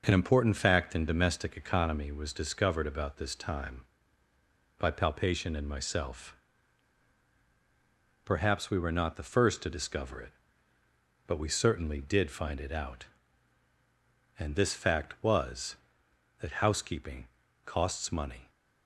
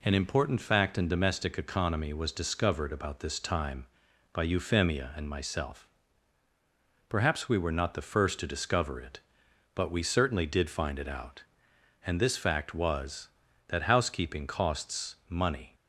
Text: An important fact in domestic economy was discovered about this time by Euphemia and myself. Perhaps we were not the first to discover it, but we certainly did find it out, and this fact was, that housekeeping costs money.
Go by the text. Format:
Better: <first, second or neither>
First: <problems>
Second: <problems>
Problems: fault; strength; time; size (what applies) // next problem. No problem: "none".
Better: second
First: says "Palpation" for "Euphemia"; at 4.9 s // pauses between "housekeeping" and "costs"; slight; at 17.2 s; 0.36 s long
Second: none